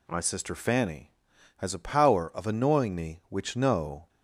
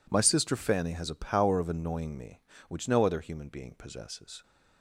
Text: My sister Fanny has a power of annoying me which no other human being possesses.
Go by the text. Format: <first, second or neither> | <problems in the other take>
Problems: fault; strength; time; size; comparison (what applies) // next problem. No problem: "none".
second | stops before "other human being possesses"; at 4.0 s